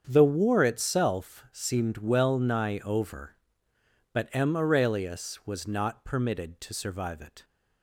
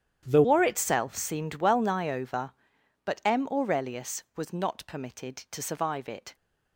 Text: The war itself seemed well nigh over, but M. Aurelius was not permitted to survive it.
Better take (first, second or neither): first